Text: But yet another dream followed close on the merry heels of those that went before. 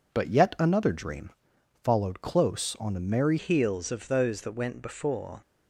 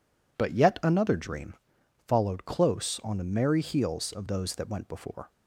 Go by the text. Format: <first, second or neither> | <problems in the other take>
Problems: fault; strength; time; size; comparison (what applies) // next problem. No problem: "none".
second | pauses between "dream" and "followed"; noticeable; at 1.3 s; 0.52 s long; noticeable in the second // changes voice at "heels"; from 3.3 s on; 2.1 s long